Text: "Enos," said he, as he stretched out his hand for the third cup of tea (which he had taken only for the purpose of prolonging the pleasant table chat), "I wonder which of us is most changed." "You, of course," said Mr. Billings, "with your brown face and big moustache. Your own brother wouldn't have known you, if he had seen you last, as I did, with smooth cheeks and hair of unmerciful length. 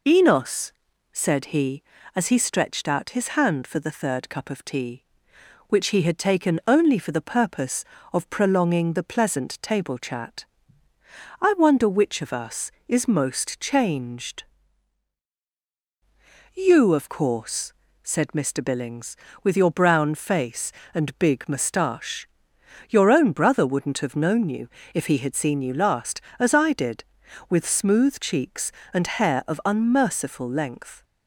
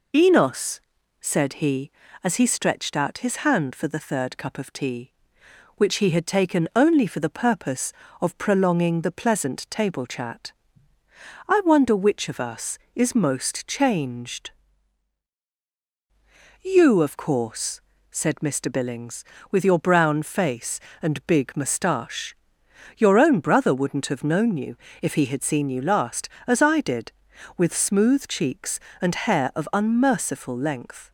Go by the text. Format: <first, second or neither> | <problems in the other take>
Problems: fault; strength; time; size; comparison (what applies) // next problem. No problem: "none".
neither | none